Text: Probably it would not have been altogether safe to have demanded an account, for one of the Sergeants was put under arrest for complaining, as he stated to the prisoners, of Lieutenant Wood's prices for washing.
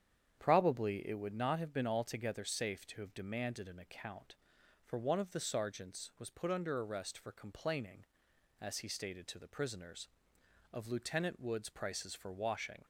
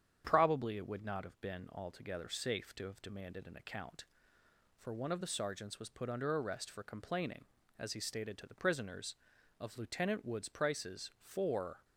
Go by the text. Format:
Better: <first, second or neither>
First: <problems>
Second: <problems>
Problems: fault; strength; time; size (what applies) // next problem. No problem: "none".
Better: first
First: starts louder than the rest; strong; until 1.4 s; 8.5 dB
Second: starts louder than the rest; strong; until 1.2 s; 8.5 dB // stops before "washing"; at 11.8 s